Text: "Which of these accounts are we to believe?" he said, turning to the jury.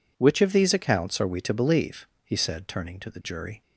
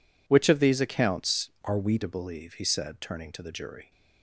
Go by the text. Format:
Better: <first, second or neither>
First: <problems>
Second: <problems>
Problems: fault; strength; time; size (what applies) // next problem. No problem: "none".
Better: first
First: none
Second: changes voice from "are" to "we"; from 1.6 to 1.9 s; 0.3 s long